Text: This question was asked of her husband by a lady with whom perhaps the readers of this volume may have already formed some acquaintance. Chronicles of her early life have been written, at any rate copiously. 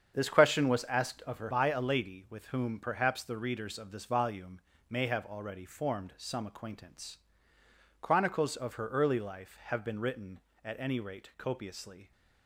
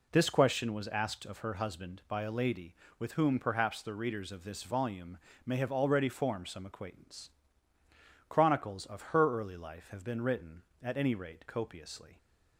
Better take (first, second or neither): second